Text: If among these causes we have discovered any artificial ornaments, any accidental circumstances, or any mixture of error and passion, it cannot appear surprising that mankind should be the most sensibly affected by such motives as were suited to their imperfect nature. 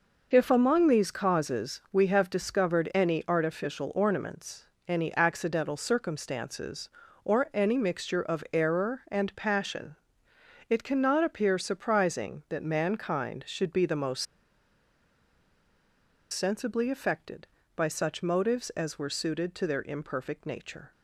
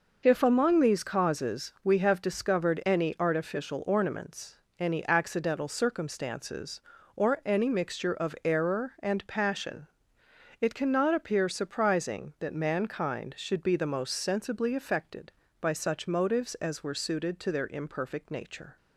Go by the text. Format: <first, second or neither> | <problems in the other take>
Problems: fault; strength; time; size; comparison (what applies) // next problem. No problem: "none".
second | pauses between "most" and "sensibly"; strong; at 14.2 s; 2.0 s long